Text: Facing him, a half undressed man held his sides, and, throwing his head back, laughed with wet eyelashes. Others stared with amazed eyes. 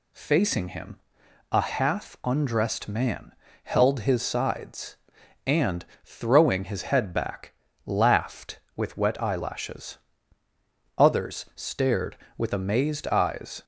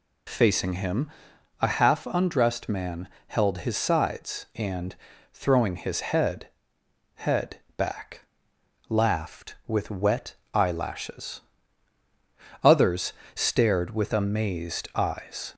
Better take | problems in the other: first | pauses between "man" and "held"; slight; at 3.0 s; 0.20 s long; slight in the first // says "head" twice; at 7.1 s // pauses between "wet" and "eyelashes"; slight; at 10.3 s; 0.16 s long // pauses between "Others" and "stared"; slight; at 13.1 s; 0.20 s long

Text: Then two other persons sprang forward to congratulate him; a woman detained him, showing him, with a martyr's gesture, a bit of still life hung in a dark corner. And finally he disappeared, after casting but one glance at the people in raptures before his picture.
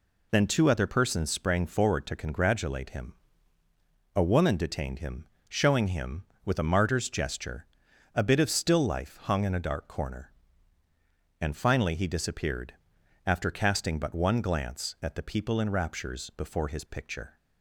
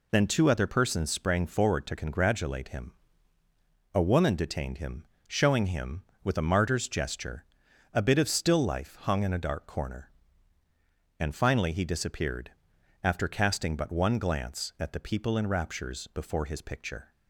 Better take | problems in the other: neither | none

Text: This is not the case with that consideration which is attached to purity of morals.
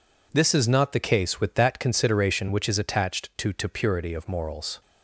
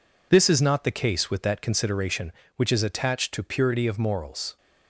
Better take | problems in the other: second | says "to" twice; at 3.5 s

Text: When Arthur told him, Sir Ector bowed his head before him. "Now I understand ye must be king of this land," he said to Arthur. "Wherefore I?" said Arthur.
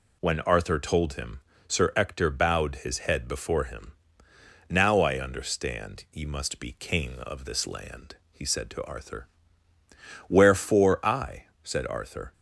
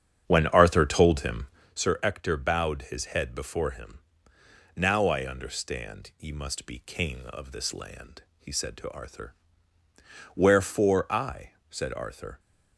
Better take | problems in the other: first | starts louder than the rest; strong; until 1.7 s; 8.5 dB

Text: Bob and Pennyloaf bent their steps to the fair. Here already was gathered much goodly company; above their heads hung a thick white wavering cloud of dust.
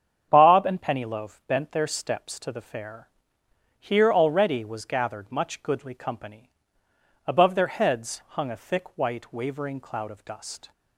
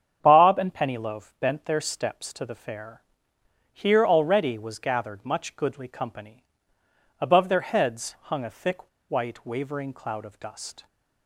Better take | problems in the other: first | starts louder than the rest; strong; until 1.2 s; 8 dB; strong in the first // pauses between "thick" and "white"; slight; at 8.8 s; 0.20 s long

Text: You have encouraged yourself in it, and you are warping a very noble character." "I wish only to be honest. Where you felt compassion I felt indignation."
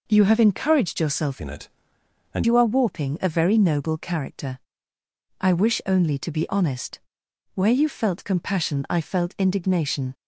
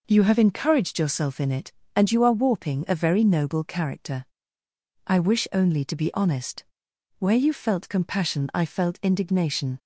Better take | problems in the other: second | changes voice from "in" to "and"; from 1.3 to 2.4 s; 1.1 s long

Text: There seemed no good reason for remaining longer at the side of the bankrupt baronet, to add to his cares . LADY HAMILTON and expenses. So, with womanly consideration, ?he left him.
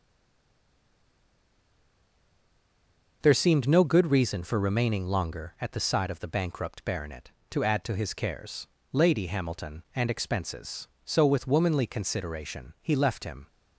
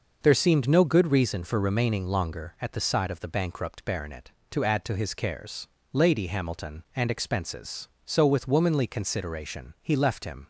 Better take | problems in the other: second | stays silent before the first word; strong; until 3.2 s; 3.2 s long

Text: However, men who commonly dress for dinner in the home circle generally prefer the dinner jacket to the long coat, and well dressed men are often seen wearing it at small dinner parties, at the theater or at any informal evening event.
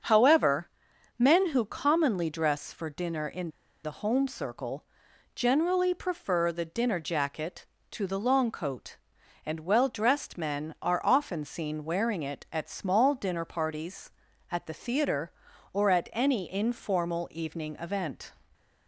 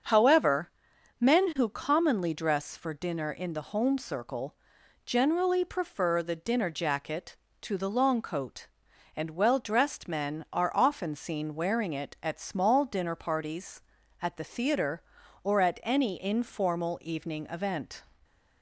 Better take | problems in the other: second | starts louder than the rest; until 1.5 s; 6.5 dB; also in the second // pauses between "in" and "the"; slight; at 3.5 s; 0.33 s long // pauses between "circle" and "generally"; noticeable; at 4.8 s; 0.50 s long; noticeable in the second

